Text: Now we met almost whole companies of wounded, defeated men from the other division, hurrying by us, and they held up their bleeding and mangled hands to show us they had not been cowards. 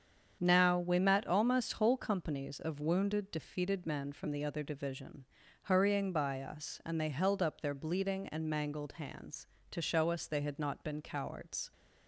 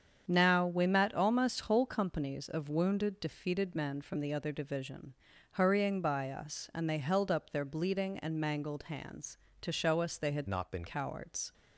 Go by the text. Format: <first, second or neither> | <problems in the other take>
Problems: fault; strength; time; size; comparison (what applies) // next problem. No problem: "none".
first | starts louder than the rest; strong; until 1.2 s; 7.5 dB; strong in the first // changes voice from "not" to "been"; from 10.4 to 10.8 s; 0.4 s long